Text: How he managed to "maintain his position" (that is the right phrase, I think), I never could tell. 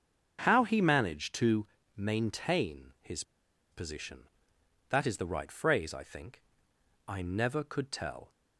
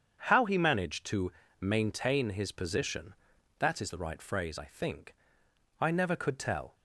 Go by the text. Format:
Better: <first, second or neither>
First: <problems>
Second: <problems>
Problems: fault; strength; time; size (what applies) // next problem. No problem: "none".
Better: second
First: starts louder than the rest; until 1.4 s; 7 dB // pauses between "to" and "maintain"; slight; at 1.6 s; 0.32 s long // pauses between "his" and "position"; noticeable; at 3.2 s; 0.47 s long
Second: starts louder than the rest; until 1.2 s; 7 dB // pauses between "to" and "maintain"; slight; at 1.3 s; 0.30 s long